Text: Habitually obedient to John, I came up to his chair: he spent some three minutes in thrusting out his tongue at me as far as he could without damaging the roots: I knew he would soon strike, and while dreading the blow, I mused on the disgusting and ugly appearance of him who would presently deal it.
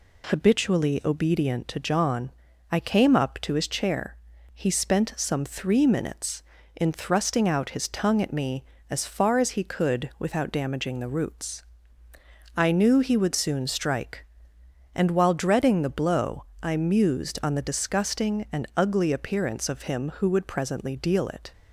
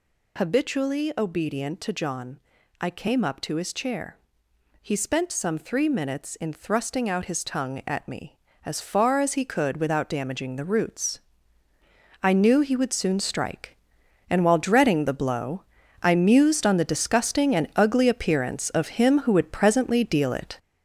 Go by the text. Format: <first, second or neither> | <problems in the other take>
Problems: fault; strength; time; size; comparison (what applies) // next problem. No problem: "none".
first | gets louder; throughout; 6.5 dB